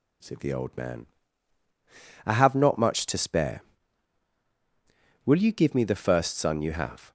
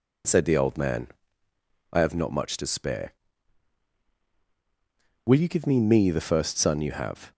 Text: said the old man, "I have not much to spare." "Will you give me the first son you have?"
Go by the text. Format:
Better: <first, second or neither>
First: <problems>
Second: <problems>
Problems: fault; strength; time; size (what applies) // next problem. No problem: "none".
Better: first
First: none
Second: says "me" twice; at 5.7 s